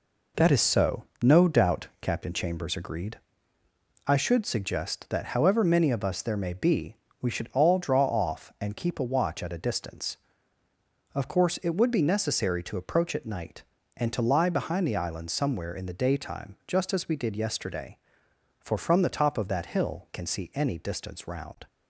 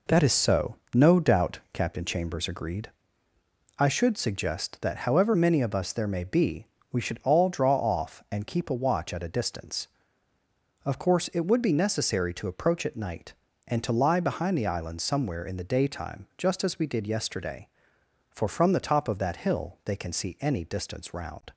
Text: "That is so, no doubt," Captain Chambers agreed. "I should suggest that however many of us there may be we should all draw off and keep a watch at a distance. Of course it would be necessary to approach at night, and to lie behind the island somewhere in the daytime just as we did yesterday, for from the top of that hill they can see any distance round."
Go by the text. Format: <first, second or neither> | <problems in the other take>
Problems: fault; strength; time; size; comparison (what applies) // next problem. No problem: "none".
second | pauses between "be" and "we"; slight; at 6.9 s; 0.24 s long; slight in the second // skips "they"; at 20.1 s